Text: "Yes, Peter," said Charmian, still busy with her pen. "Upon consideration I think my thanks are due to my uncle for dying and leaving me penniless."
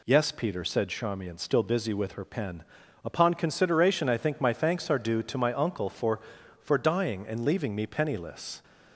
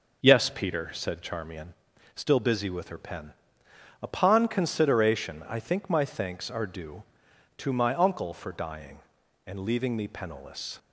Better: second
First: says "for" twice; at 6.6 s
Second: none

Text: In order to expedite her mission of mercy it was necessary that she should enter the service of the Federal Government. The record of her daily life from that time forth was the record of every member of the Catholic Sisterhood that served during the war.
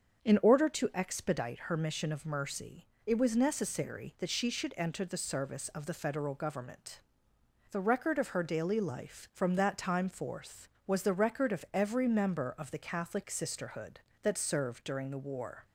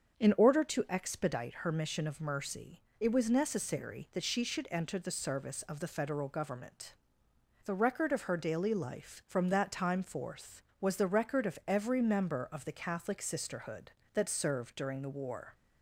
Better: neither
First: starts louder than the rest; until 1.3 s; 7 dB // pauses between "mercy" and "it"; slight; at 2.8 s; 0.20 s long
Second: starts louder than the rest; until 1.2 s; 7 dB // pauses between "mercy" and "it"; slight; at 2.8 s; 0.18 s long

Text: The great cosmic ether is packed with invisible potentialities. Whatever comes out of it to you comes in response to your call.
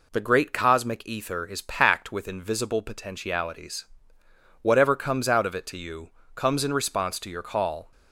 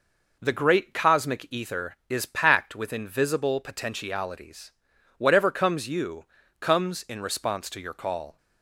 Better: first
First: pauses between "you" and "comes"; slight; at 6.1 s; 0.23 s long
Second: skips "out of it to"; at 5.8 s // pauses between "you" and "comes"; slight; at 6.2 s; 0.36 s long

